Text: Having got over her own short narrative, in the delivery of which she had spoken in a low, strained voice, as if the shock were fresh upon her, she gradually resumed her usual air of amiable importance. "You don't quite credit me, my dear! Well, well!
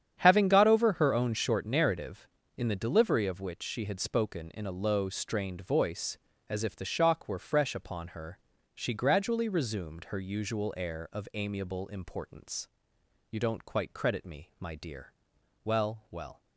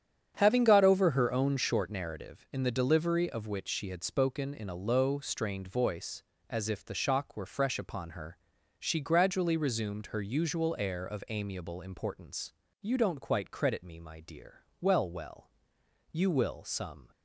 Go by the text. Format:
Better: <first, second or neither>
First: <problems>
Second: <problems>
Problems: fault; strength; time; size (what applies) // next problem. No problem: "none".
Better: first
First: starts louder than the rest; strong; until 1.2 s; 9 dB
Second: starts louder than the rest; strong; until 1.3 s; 9 dB // goes on to say "You will some"; noticeable; from 16.1 s on; 1.0 s long